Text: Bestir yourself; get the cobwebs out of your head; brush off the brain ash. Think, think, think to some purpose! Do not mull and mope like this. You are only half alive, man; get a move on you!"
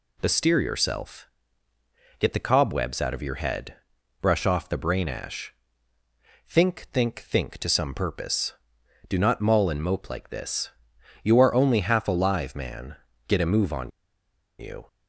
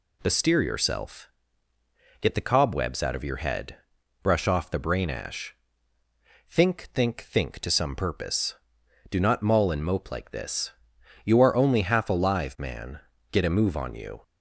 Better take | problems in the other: second | pauses between "on" and "you"; noticeable; at 13.9 s; 0.68 s long

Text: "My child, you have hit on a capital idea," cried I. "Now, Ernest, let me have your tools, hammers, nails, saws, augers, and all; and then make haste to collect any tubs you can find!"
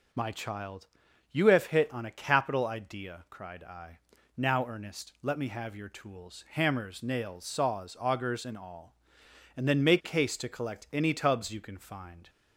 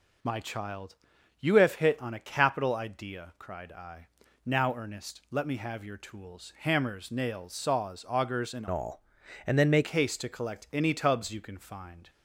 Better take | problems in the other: first | changes voice from "all" to "make"; from 8.7 to 9.8 s; 1.1 s long

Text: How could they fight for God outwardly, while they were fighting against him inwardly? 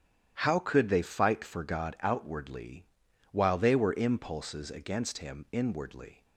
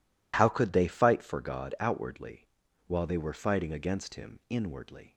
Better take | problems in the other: second | starts louder than the rest; strong; until 1.4 s; 10.5 dB // says "impulses" for "fighting"; at 3.9 s

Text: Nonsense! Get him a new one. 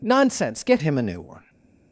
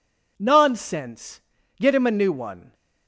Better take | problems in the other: second | changes voice at "him"; from 0.8 s on; 0.6 s long // stays silent after the last word; slight; from 1.4 s on; 0.5 s long

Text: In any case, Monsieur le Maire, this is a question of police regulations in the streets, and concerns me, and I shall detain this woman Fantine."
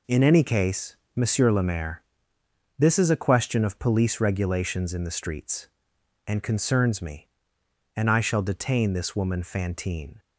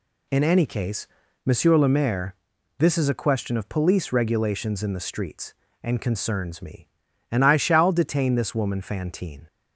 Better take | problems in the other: neither | none

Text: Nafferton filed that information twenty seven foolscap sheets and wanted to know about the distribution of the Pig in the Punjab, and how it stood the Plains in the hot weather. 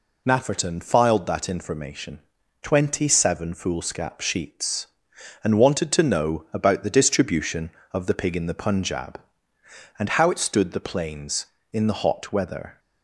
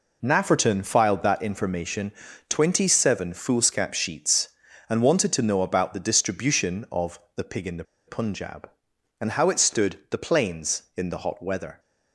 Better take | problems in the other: first | pauses between "information" and "twenty"; slight; at 2.1 s; 0.36 s long; also in the first // pauses between "of" and "the"; slight; at 7.1 s; 0.18 s long // pauses between "the" and "Punjab"; slight; at 7.8 s; 0.24 s long

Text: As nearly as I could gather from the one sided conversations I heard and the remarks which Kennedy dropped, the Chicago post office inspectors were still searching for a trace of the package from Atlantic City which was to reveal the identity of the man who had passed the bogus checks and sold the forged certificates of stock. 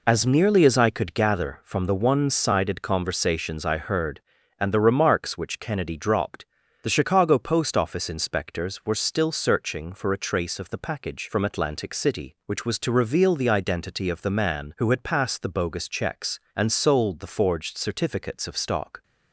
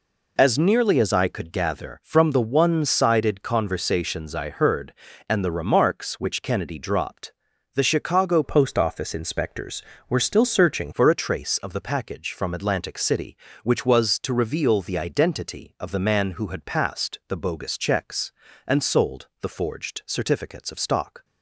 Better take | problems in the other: first | changes voice from "post" to "searching"; from 8.4 to 10.9 s; 2.5 s long

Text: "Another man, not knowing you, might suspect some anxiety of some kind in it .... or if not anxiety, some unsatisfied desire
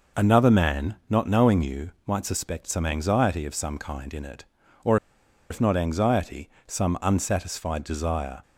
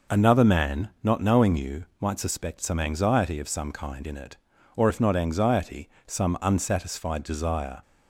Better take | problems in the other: second | pauses between "or" and "if"; noticeable; at 4.9 s; 0.54 s long

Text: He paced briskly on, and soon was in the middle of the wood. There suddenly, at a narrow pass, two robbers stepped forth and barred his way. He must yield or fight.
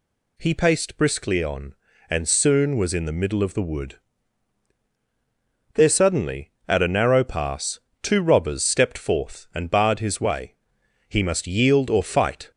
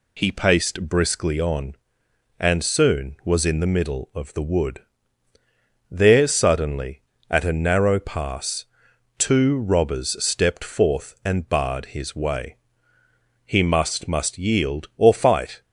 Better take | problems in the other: first | says "must" twice; at 14.0 s

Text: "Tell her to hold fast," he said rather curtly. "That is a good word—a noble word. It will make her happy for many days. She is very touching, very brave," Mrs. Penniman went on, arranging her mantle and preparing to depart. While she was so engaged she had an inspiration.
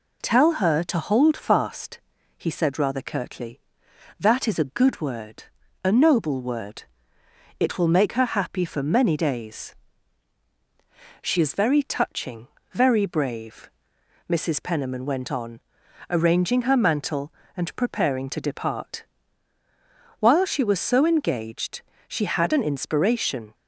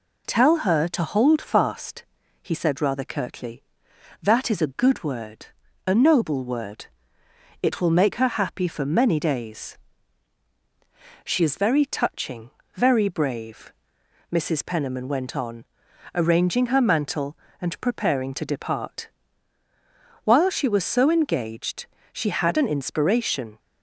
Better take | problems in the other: neither | pauses between "engaged" and "she"; slight; the same in both

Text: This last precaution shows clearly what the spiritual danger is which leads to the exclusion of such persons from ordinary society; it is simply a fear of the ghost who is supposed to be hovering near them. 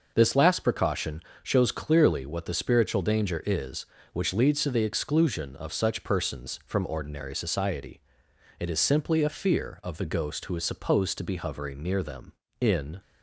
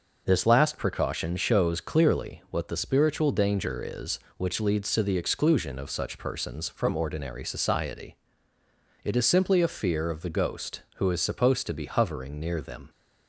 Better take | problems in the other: second | pauses between "precaution" and "shows"; slight; at 1.2 s; 0.18 s long // goes on to say "In"; slight; from 12.6 s on; 0.38 s long

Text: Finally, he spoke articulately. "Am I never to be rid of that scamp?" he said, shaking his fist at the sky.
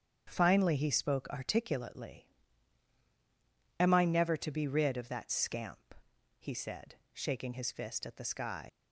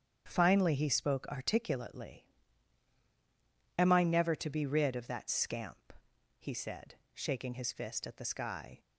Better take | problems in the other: second | starts louder than the rest; strong; until 1.2 s; 8 dB; strong in the second // leaves "sky" unfinished; at 8.6 s; 105 ms

